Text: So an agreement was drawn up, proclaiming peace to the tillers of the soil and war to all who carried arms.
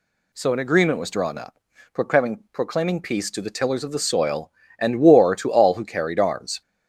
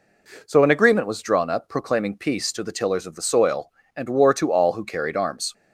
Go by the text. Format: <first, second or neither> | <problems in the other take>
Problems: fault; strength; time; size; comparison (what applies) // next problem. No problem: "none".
second | says "proclaiming" twice; at 2.5 s